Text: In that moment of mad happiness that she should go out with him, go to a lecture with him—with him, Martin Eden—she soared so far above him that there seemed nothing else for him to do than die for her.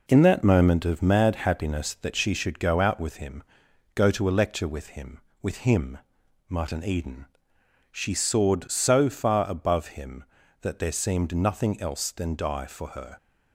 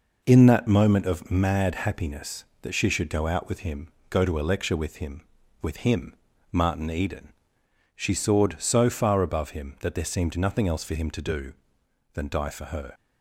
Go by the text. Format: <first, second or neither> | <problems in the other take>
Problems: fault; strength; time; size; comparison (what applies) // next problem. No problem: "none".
second | skips "for him to do"; at 12.1 s